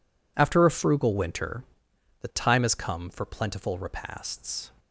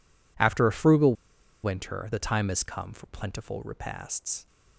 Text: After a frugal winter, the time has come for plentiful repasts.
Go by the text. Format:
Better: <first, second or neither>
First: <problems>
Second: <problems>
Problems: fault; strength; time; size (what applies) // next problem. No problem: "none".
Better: first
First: none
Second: pauses between "frugal" and "winter"; noticeable; at 1.1 s; 0.49 s long